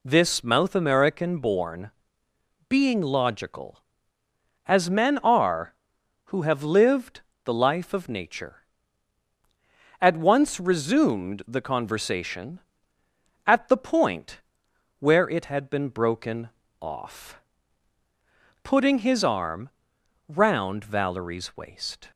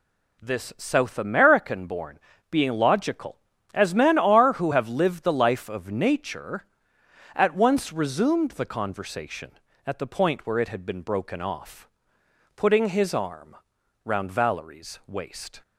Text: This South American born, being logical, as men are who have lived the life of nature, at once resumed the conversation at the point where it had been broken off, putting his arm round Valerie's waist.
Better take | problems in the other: second | says "Mouth" for "South"; at 0.4 s // pauses between "lived" and "the"; slight; at 7.2 s; 0.22 s long // pauses between "point" and "where"; noticeable; at 14.3 s; 0.60 s long // pauses between "broken" and "off"; slight; at 16.4 s; 0.30 s long // pauses between "arm" and "round"; noticeable; at 19.7 s; 0.58 s long; noticeable in the second

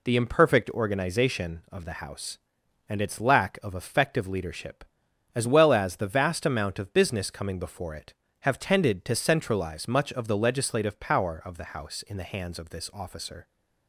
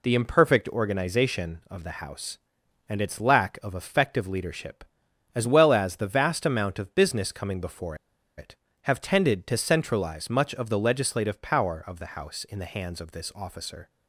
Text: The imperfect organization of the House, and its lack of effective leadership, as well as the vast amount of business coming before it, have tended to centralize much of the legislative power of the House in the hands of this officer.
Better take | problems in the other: first | pauses between "before" and "it"; at 7.9 s; 0.42 s long

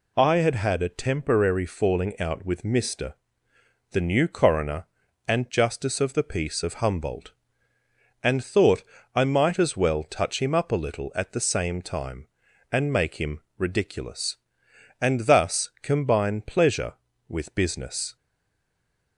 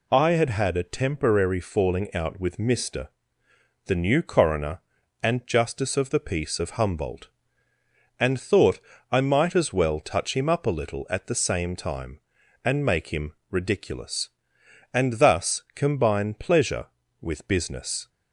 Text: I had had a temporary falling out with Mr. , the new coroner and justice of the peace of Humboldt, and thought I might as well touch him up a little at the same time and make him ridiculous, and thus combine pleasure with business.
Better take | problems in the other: second | pauses between "thought" and "I"; slight; at 8.8 s; 0.32 s long; slight in the second // pauses between "him" and "ridiculous"; slight; at 13.4 s; 0.16 s long; slight in the second // stays silent after the last word; from 18.1 s on; 1.0 s long

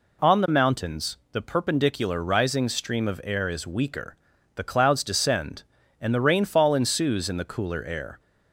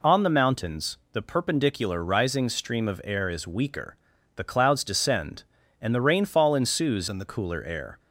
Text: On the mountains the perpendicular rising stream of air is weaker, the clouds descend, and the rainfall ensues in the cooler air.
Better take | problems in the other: first | changes voice from "in" to "the"; from 7.0 to 7.2 s; 0.2 s long

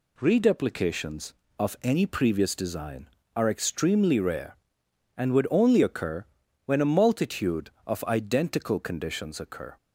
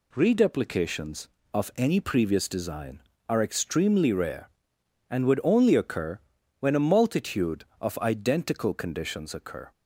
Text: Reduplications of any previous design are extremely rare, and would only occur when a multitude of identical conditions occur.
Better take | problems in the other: neither | pauses between "occur" and "when"; the same in both

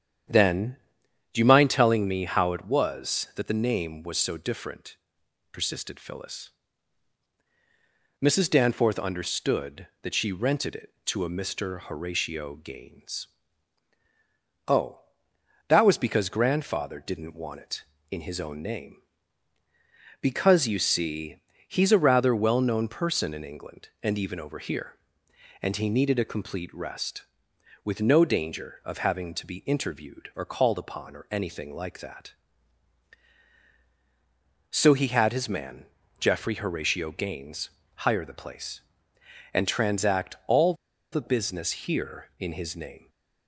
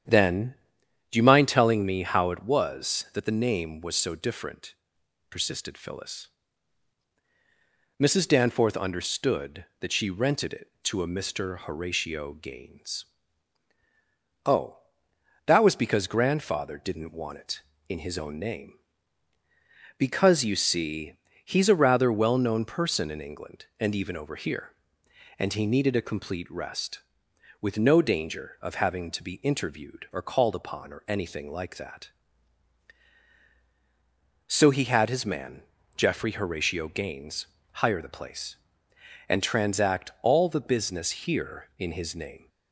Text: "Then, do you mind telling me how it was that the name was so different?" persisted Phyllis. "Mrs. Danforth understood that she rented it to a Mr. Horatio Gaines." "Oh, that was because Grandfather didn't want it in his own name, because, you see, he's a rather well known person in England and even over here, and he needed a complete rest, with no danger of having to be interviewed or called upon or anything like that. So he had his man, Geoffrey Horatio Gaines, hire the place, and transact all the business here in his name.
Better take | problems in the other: second | starts louder than the rest; strong; until 1.8 s; 9.5 dB; strong in the second // pauses between "all" and "the"; at 40.7 s; 0.38 s long

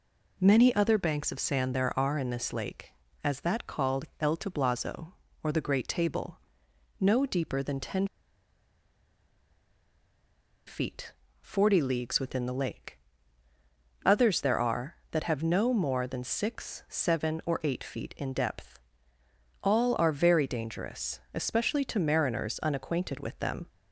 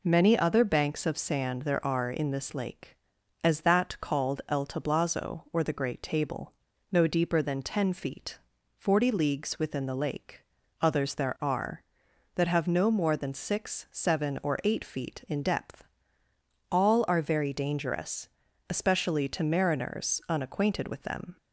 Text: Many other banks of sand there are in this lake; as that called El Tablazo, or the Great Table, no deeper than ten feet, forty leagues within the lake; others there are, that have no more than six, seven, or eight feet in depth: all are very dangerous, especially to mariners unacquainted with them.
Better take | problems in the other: second | pauses between "called" and "El"; slight; at 4.0 s; 0.16 s long // pauses between "ten" and "feet"; strong; at 8.0 s; 2.6 s long

